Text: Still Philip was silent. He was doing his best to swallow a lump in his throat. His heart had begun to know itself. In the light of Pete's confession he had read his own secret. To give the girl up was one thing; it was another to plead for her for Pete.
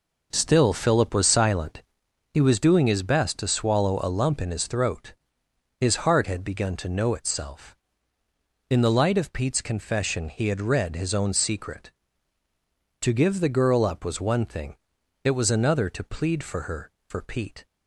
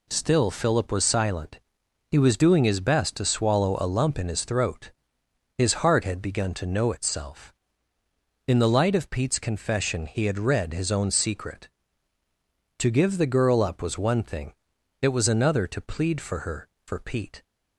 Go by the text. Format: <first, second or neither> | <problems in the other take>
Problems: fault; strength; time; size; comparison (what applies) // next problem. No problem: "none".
second | starts louder than the rest; noticeable; until 2.0 s; 5 dB